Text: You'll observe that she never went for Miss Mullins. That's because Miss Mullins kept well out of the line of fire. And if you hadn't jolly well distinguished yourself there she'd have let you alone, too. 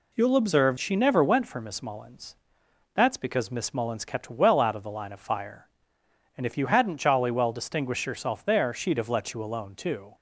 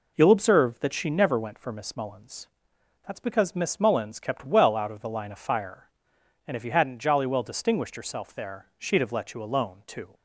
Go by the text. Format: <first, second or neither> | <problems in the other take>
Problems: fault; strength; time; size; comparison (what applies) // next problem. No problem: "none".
second | skips "that"; at 0.7 s